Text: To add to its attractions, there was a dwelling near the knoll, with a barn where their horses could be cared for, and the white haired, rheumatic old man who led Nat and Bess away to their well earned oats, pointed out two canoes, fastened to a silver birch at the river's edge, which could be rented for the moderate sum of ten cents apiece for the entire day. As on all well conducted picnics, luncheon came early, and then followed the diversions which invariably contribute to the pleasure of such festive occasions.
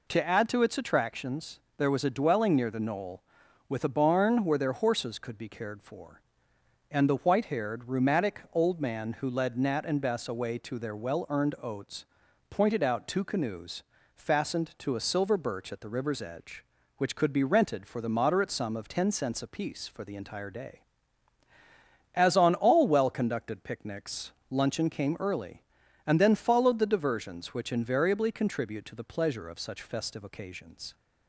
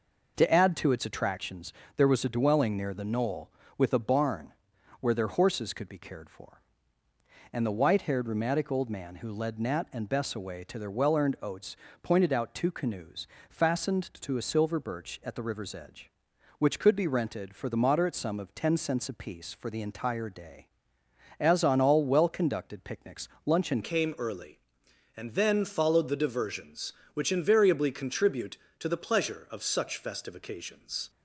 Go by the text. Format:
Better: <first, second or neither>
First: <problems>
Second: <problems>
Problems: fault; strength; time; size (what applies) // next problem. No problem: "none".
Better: first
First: none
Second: pauses between "barn" and "where"; noticeable; at 4.5 s; 0.46 s long // changes voice at "came"; from 23.8 s on; 7.2 s long